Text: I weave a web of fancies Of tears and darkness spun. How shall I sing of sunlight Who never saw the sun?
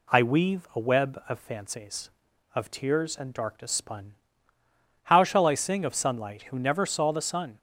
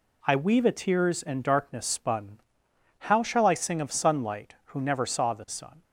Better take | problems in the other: first | skips "web of fancies Of"; at 0.7 s

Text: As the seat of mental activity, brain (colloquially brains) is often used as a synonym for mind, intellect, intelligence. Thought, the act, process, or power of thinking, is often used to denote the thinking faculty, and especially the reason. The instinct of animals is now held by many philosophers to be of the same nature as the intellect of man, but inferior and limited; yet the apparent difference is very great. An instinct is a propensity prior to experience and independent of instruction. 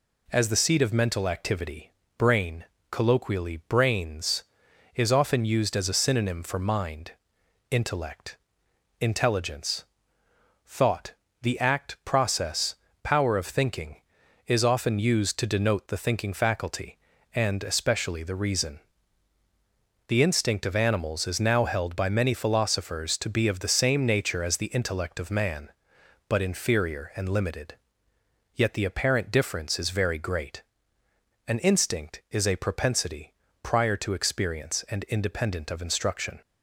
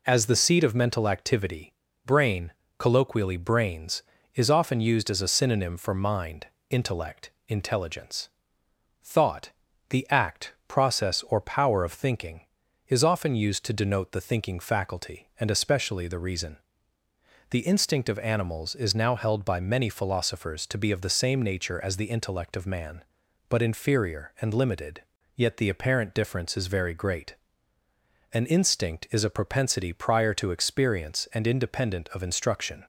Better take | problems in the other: second | skips "or"; at 12.8 s // pauses between "propensity" and "prior"; slight; at 33.3 s; 0.30 s long

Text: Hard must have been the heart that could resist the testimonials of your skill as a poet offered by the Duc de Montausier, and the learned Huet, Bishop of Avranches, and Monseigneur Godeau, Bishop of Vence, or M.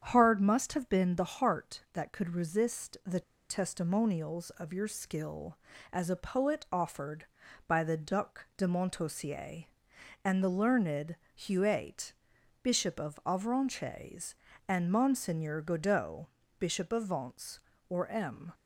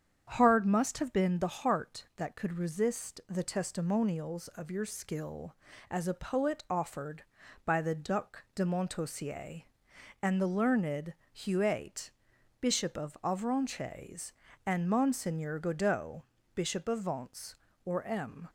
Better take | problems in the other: second | starts louder than the rest; strong; until 1.0 s; 8 dB; strong in the second // pauses between "the" and "testimonials"; slight; at 3.2 s; 0.28 s long // pauses between "learned" and "Huet"; slight; at 11.1 s; 0.18 s long; slight in the second

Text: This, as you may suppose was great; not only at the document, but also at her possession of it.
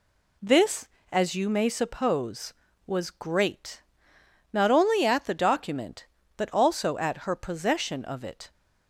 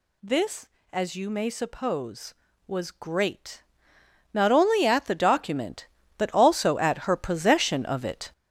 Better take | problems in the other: first | gets louder; strong; throughout; 7.5 dB

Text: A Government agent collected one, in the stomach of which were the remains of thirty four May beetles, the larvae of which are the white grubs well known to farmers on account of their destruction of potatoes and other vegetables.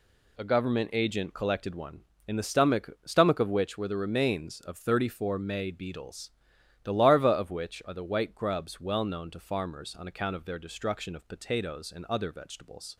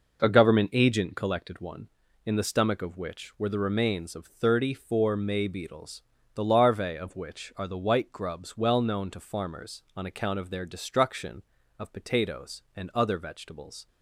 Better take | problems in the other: second | says "stomach" twice; at 3.0 s

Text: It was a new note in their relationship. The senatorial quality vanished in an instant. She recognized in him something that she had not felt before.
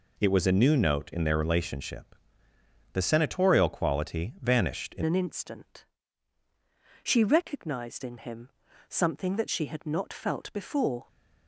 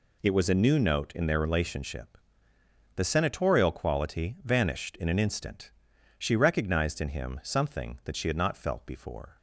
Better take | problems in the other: second | changes voice at "an"; from 5.0 s on; 6.0 s long // pauses between "him" and "something"; at 8.4 s; 0.38 s long

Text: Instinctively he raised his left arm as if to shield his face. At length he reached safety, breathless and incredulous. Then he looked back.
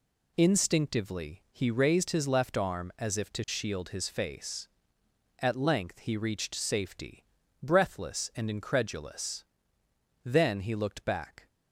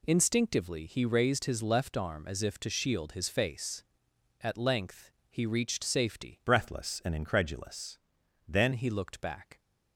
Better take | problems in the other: first | pauses between "length" and "he"; slight; at 5.1 s; 0.20 s long // changes voice from "breathless" to "Then"; from 6.4 to 8.7 s; 2.3 s long

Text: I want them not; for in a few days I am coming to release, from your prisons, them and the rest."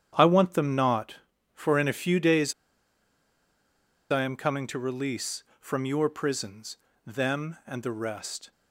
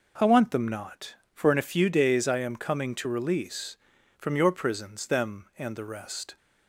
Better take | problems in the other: second | starts louder than the rest; strong; until 1.5 s; 9 dB // pauses between "days" and "I"; strong; at 2.5 s; 1.5 s long

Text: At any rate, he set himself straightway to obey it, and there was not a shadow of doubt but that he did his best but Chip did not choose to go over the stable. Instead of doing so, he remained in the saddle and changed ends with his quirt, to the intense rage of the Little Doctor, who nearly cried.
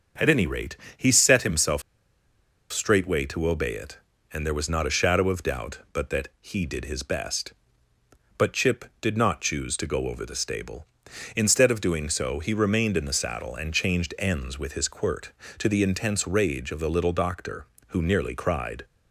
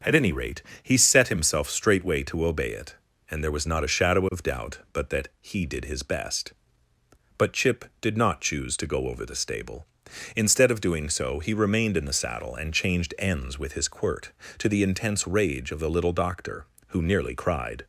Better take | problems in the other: second | starts louder than the rest; until 1.3 s; 6.5 dB; also in the second // pauses between "himself" and "straightway"; noticeable; at 1.8 s; 0.90 s long

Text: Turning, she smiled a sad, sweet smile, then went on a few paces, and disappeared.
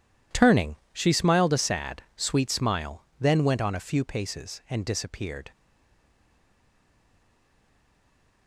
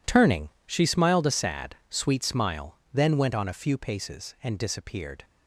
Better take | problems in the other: second | stays silent after the last word; strong; from 5.5 s on; 2.9 s long

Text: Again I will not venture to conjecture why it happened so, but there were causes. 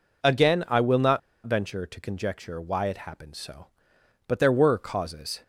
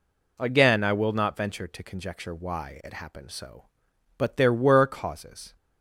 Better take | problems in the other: second | pauses between "not" and "venture"; slight; at 1.1 s; 0.26 s long

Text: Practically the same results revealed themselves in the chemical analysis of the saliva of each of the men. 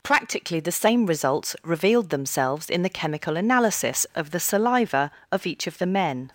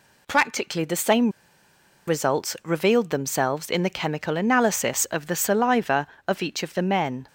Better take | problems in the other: first | pauses between "same" and "results"; noticeable; at 1.2 s; 0.78 s long

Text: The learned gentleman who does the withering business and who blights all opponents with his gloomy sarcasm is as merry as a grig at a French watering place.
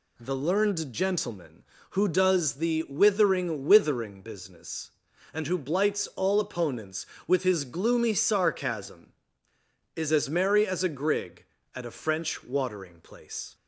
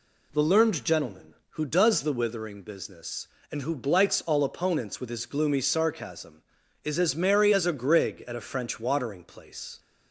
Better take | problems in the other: second | says "withering" twice; at 3.6 s

